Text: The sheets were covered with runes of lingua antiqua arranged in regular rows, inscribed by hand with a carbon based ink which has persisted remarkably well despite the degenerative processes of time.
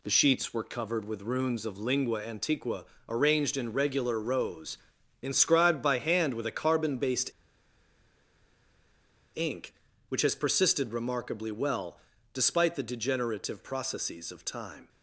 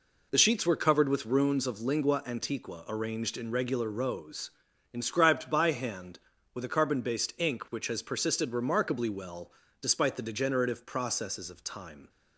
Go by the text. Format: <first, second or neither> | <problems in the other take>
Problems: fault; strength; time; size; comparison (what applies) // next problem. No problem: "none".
second | pauses between "antiqua" and "arranged"; slight; at 2.8 s; 0.22 s long // pauses between "based" and "ink"; strong; at 7.3 s; 2.0 s long // pauses between "well" and "despite"; slight; at 11.9 s; 0.36 s long; slight in the second